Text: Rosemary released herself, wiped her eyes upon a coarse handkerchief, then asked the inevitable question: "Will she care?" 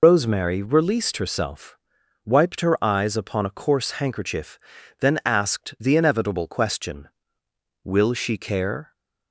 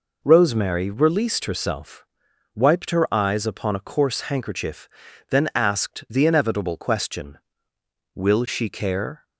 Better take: second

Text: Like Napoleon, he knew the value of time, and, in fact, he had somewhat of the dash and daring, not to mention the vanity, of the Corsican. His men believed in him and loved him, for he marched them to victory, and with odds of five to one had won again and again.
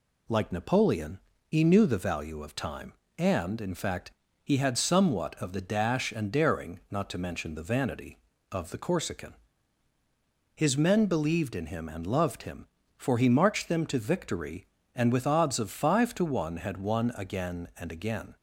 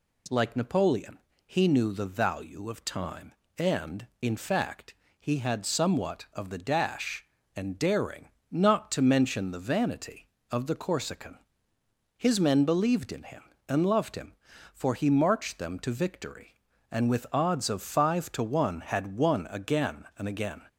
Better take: neither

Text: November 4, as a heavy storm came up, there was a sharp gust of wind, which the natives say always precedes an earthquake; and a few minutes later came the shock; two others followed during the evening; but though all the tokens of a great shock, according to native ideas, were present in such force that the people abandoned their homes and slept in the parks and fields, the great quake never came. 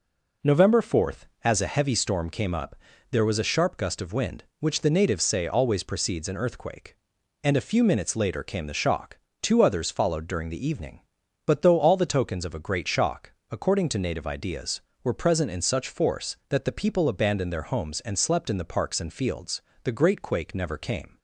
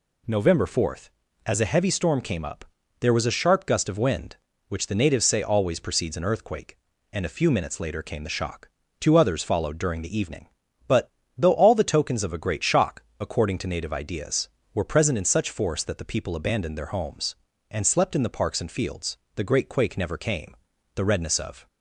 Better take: first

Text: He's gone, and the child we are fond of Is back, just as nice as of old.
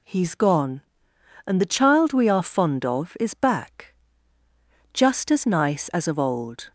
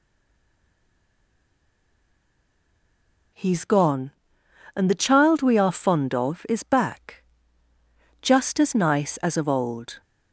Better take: first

